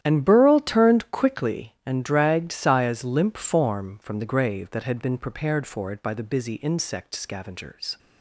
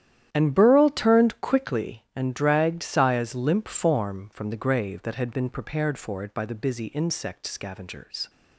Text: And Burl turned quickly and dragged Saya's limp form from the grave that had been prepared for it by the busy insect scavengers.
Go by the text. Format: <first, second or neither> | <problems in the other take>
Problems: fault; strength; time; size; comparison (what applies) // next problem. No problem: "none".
neither | starts louder than the rest; strong; the same in both